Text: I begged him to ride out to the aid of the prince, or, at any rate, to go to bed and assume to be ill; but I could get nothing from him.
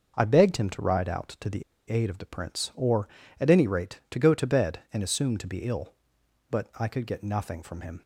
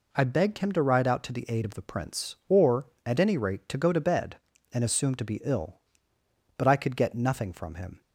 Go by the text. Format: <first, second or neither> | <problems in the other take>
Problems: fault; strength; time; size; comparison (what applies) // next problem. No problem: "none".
second | starts louder than the rest; until 1.1 s; 6 dB // pauses between "the" and "aid"; slight; at 1.6 s; 0.26 s long